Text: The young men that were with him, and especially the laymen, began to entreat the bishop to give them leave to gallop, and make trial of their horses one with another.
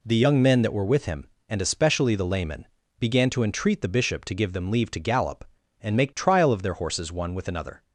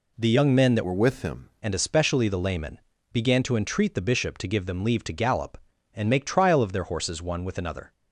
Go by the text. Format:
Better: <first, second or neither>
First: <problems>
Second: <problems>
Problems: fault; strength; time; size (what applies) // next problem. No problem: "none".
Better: first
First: none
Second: changes voice from "were" to "him"; from 0.8 to 1.4 s; 0.6 s long